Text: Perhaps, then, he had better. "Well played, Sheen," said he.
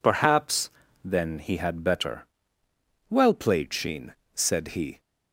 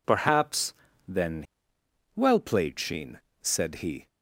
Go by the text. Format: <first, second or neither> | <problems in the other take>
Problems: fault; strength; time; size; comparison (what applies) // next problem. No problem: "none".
first | skips "he had better"; at 1.7 s